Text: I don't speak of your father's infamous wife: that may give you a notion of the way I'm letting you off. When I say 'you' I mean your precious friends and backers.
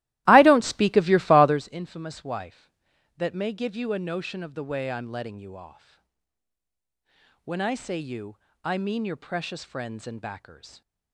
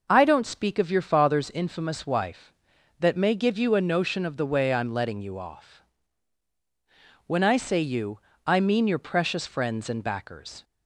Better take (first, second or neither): second